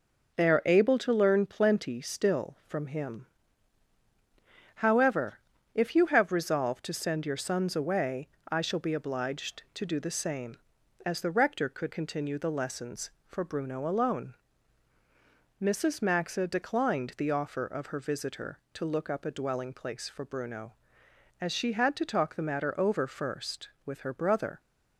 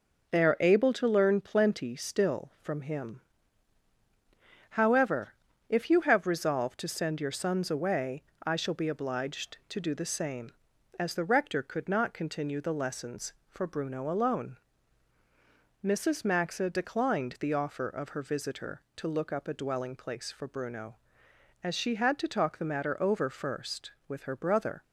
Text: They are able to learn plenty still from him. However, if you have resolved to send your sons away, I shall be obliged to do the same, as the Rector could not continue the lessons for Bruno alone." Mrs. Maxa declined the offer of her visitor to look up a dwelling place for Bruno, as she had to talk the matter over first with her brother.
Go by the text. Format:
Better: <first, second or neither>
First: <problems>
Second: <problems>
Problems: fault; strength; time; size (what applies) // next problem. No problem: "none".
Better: second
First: skips "not"; at 11.9 s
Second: none